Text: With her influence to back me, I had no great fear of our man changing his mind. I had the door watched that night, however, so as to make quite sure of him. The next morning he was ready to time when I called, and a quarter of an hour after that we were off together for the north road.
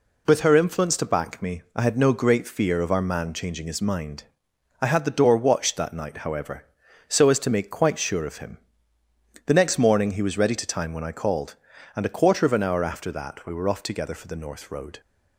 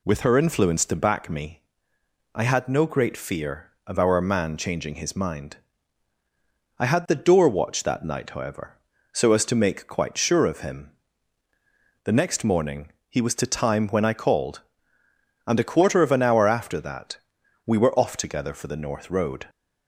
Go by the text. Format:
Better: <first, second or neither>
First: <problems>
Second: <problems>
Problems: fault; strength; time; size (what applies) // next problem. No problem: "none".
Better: first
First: none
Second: pauses between "morning" and "he"; slight; at 12.8 s; 0.20 s long // skips "ready"; at 13.3 s // pauses between "that" and "we"; noticeable; at 17.1 s; 0.48 s long